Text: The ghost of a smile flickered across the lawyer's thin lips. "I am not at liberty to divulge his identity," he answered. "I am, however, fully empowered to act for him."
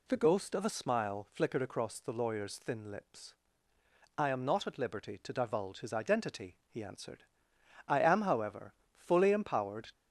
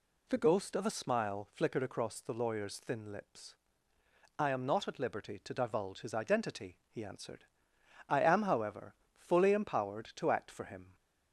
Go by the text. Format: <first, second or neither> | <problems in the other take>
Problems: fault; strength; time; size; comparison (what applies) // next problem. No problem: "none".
second | stops before "to act for him"; at 9.9 s